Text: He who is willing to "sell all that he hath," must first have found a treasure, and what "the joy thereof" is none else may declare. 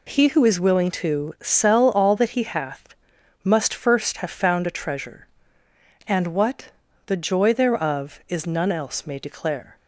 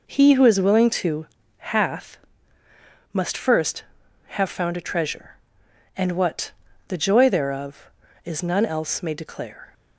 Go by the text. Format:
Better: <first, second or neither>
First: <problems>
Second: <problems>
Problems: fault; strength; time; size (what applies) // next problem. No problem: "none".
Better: first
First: pauses between "what" and "the"; slight; at 6.7 s; 0.36 s long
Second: skips "sell all that he"; at 1.4 s // pauses between "what" and "the"; at 6.5 s; 0.38 s long